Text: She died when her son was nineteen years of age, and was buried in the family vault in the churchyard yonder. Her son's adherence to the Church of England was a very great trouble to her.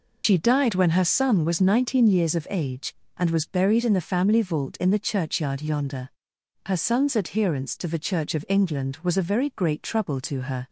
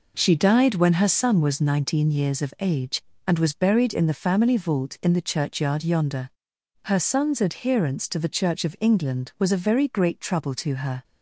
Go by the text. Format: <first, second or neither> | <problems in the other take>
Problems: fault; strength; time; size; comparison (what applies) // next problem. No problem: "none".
second | loses the start of "She"; at 0.2 s; 85 ms